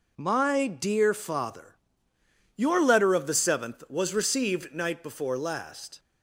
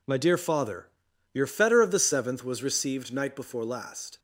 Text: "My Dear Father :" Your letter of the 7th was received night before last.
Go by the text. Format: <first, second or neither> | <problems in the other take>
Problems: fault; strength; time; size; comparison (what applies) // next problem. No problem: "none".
first | says "fetter" for "letter"; at 1.4 s